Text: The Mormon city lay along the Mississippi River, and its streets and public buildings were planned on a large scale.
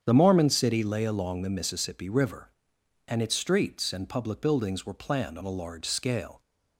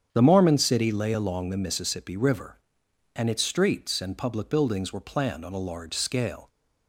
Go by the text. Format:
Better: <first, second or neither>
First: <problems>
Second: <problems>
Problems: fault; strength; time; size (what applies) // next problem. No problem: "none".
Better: neither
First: starts louder than the rest; strong; until 1.0 s; 8.5 dB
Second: starts louder than the rest; strong; until 1.1 s; 8.5 dB